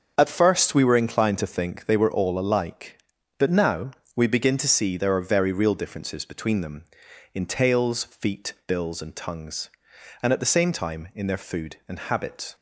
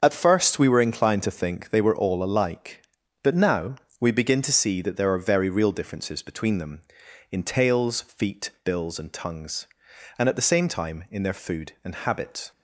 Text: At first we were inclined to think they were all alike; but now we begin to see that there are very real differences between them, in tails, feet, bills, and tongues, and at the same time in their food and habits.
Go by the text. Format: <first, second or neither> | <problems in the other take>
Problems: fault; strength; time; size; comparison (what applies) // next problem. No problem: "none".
second | starts louder than the rest; until 1.1 s; 6 dB; also in the second // pauses between "now" and "we"; slight; at 3.9 s; 0.22 s long; slight in the second // skips "that"; at 4.9 s